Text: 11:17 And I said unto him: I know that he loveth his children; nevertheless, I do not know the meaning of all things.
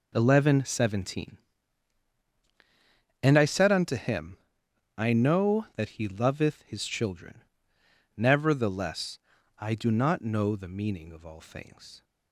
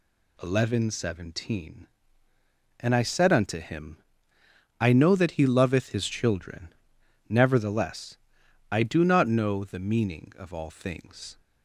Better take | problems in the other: neither | none

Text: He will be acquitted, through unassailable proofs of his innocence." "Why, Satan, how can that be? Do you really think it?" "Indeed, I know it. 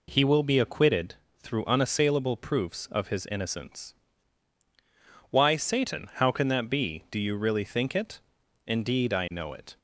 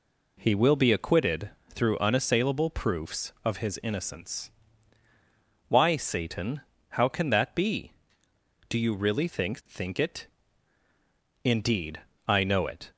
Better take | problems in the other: first | says "think" twice; at 9.6 s

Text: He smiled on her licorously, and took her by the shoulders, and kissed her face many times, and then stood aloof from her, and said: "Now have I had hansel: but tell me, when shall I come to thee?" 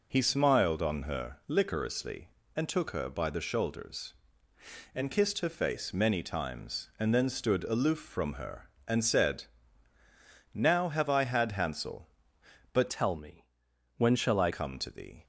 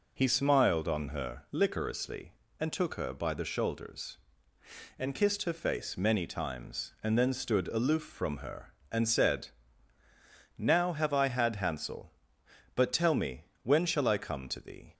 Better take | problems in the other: second | changes voice from "tell" to "I"; from 12.8 to 14.5 s; 1.7 s long

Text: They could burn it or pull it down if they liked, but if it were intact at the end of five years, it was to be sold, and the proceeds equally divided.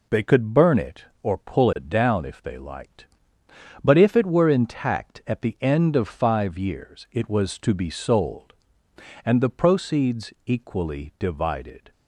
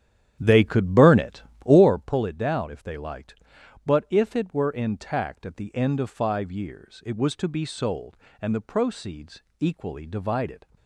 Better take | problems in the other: first | starts louder than the rest; strong; until 2.1 s; 10.5 dB // pauses between "proceeds" and "equally"; slight; at 9.4 s; 0.18 s long

